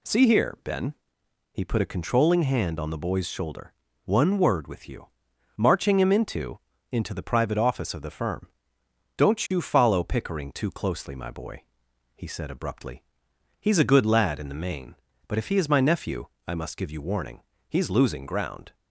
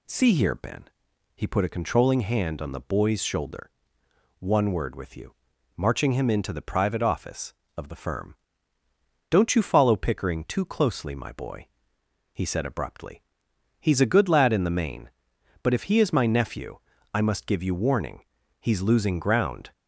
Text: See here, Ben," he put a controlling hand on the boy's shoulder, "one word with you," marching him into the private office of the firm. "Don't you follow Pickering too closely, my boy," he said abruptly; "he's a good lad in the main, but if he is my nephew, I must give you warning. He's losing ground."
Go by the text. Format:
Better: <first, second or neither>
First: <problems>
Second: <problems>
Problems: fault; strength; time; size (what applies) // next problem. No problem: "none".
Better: second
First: says "into" twice; at 6.9 s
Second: none